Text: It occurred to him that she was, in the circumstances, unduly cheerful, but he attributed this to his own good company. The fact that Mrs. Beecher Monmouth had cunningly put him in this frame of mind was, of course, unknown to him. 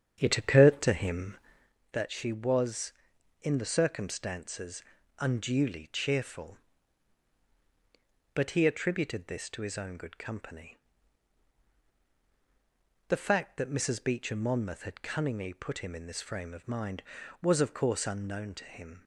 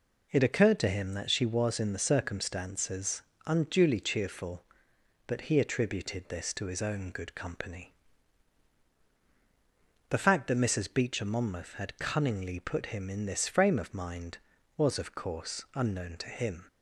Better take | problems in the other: second | starts louder than the rest; strong; until 1.7 s; 8.5 dB

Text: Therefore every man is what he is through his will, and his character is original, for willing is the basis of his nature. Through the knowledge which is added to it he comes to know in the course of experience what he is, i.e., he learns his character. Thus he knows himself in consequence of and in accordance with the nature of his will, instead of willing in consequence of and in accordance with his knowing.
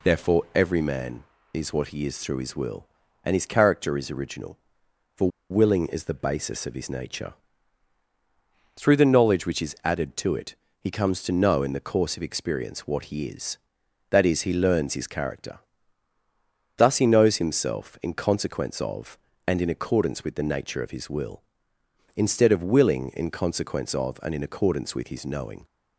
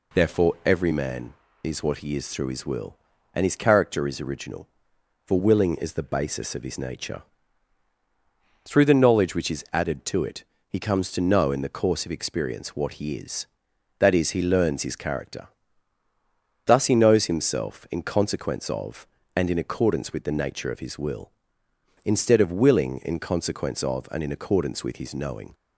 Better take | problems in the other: second | pauses between "for" and "willing"; slight; at 5.2 s; 0.20 s long // pauses between "it" and "he"; slight; at 10.5 s; 0.24 s long; slight in the second

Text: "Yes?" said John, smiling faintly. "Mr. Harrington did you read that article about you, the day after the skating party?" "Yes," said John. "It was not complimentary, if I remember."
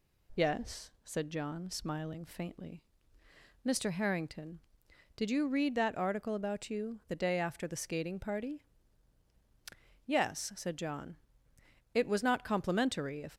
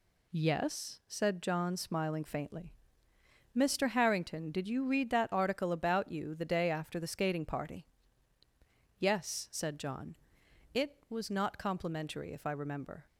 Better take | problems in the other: second | stops before "I remember"; at 13.3 s

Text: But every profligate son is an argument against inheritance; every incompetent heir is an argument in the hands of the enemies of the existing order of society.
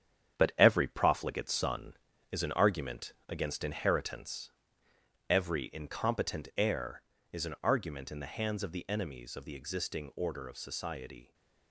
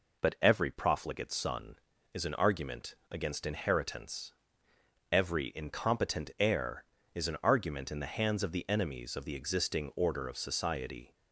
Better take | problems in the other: second | gets quieter; throughout; 6.5 dB // pauses between "argument" and "against"; slight; at 3.1 s; 0.16 s long; slight in the second

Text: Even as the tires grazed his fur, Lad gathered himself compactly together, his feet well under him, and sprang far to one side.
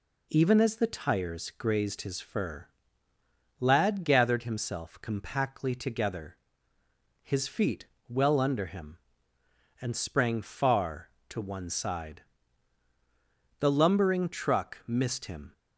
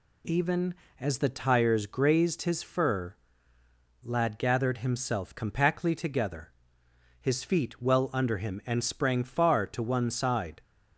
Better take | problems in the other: second | pauses between "feet" and "well"; slight; at 7.8 s; 0.22 s long // goes on to say "The lumbering truck missed him"; strong; from 13.5 s on; 1.9 s long

